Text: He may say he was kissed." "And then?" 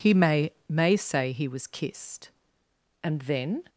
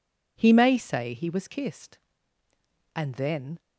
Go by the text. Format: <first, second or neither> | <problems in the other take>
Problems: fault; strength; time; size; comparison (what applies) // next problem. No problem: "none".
second | says "may" twice; at 0.6 s